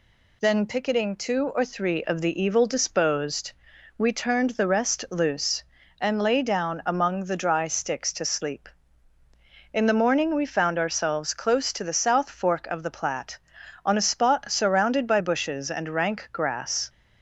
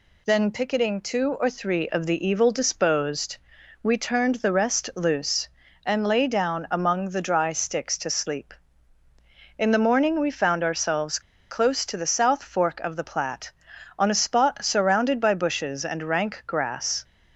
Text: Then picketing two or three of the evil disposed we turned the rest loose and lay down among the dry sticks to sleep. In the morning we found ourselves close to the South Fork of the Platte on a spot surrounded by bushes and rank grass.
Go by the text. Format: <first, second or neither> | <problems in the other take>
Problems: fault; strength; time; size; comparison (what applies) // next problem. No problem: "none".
first | pauses between "disposed" and "we"; at 3.3 s; 0.44 s long; also in the first // pauses between "ourselves" and "close"; slight; at 11.1 s; 0.30 s long